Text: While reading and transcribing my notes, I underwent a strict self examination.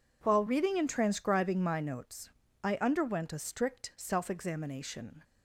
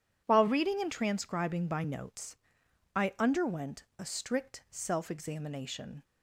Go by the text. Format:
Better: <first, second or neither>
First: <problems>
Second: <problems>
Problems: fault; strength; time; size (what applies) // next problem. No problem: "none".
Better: first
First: none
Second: says "by" for "my"; at 1.6 s